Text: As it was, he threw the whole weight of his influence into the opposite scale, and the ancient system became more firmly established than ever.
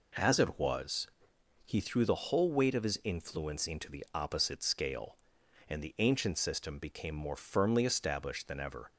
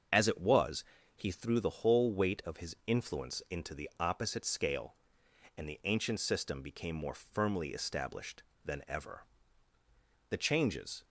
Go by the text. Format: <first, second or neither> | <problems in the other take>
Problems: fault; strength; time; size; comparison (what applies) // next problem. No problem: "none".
first | starts louder than the rest; until 1.4 s; 6.5 dB // goes on to say "The changes"; noticeable; from 10.2 s on; 0.74 s long